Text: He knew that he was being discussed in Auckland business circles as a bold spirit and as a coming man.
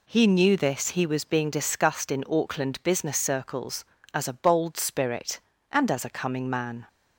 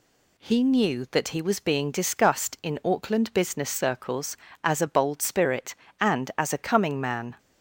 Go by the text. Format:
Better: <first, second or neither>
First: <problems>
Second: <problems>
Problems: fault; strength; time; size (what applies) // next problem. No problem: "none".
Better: second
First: says "this" for "that"; at 0.5 s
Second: none